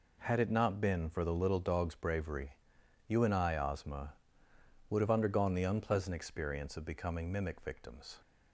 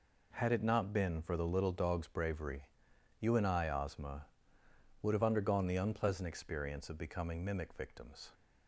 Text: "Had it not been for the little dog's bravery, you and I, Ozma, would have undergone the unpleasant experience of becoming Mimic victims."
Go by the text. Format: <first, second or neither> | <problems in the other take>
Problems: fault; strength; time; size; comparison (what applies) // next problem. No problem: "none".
neither | none